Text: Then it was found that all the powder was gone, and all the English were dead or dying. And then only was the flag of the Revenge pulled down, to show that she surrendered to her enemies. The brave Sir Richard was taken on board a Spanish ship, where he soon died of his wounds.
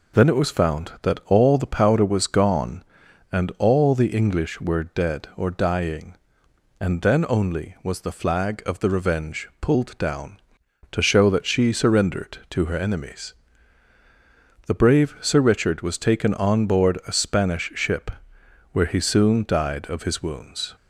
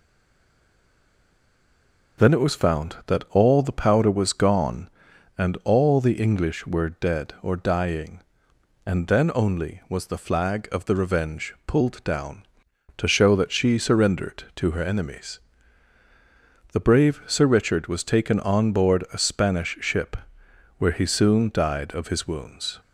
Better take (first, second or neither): first